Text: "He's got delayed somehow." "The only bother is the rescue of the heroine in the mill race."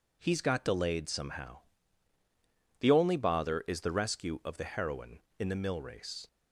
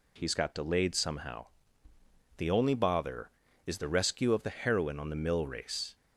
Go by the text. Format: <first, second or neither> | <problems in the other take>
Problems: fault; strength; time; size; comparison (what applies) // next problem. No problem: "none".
first | says "on" for "in"; at 4.9 s